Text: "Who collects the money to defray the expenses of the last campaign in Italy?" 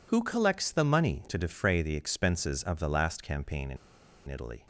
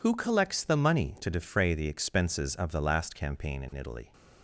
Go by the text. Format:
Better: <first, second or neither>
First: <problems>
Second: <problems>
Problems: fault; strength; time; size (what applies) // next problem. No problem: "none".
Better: second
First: pauses between "in" and "Italy"; noticeable; at 3.7 s; 0.51 s long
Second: none